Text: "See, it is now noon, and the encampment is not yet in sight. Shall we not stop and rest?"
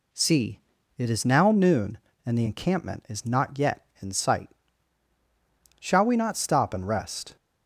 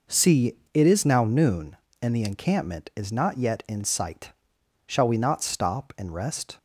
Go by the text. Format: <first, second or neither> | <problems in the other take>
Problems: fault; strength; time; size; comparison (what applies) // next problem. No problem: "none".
neither | none